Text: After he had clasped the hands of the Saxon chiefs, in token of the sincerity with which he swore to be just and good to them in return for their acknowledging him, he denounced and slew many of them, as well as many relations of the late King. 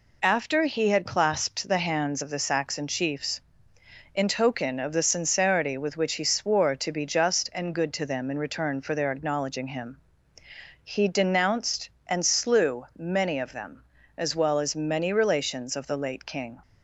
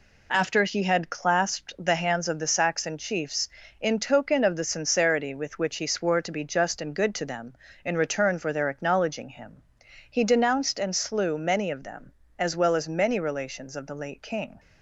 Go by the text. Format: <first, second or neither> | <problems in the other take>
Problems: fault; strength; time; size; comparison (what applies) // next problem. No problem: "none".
first | gets quieter; throughout; 6.5 dB